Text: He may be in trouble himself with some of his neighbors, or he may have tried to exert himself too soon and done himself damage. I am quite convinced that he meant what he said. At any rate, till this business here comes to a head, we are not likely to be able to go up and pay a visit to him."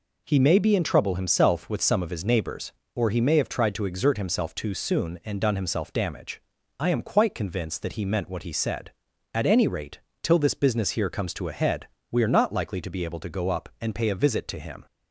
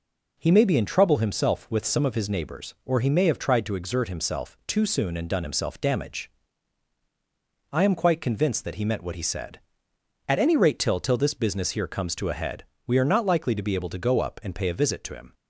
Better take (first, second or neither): first